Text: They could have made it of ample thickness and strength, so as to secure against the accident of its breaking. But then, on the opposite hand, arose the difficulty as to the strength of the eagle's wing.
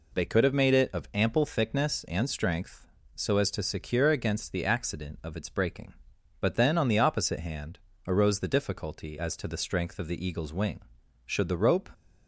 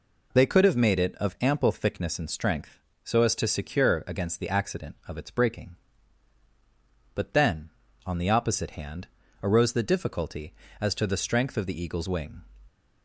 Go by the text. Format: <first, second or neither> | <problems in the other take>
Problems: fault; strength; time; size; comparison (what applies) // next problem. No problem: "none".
second | goes on to say "Should the rope"; noticeable; from 11.2 s on; 0.64 s long